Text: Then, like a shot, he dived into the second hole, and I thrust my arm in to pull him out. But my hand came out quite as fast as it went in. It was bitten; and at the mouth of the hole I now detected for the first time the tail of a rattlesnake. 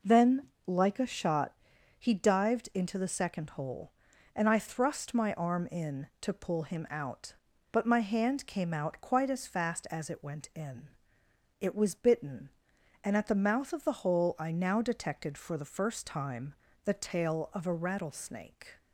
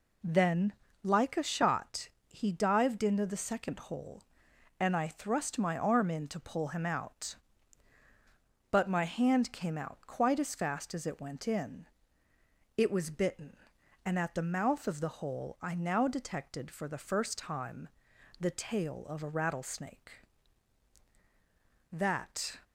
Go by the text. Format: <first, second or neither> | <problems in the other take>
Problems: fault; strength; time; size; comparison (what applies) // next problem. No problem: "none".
first | pauses between "time" and "the"; noticeable; at 17.8 s; 0.54 s long; slight in the first // goes on to say "That"; noticeable; from 21.9 s on; 0.66 s long